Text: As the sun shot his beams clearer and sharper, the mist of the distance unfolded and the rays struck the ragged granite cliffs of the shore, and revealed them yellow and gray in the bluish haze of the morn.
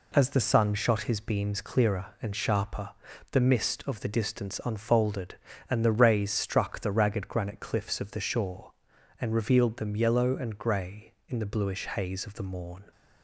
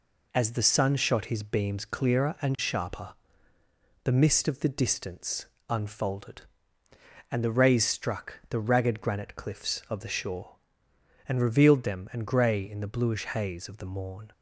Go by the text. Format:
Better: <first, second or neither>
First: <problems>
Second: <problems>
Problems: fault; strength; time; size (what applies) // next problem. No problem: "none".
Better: first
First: none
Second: pauses between "distance" and "unfolded"; slight; at 5.4 s; 0.24 s long // skips "yellow"; at 12.0 s